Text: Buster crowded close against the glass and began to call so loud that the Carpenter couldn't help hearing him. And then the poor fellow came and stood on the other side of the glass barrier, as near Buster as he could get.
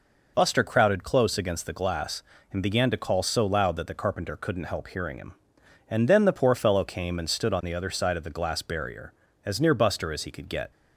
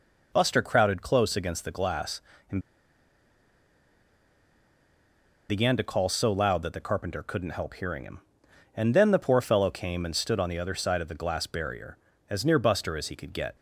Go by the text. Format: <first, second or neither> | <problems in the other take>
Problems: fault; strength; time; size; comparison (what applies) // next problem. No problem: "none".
first | pauses between "and" and "began"; strong; at 2.5 s; 2.8 s long